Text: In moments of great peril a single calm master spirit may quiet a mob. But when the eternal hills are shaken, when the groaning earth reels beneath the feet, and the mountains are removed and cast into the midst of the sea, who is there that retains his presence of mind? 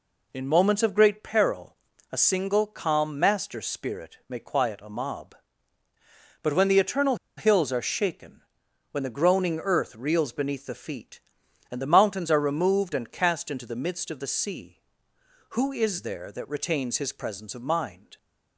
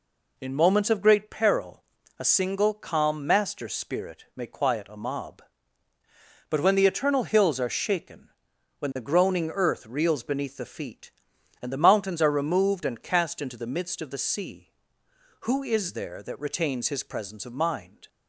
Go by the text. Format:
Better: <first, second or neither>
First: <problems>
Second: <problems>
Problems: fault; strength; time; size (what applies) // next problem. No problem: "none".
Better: second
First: pauses between "peril" and "a"; slight; at 1.7 s; 0.36 s long // pauses between "eternal" and "hills"; slight; at 7.1 s; 0.21 s long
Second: pauses between "peril" and "a"; slight; at 1.8 s; 0.36 s long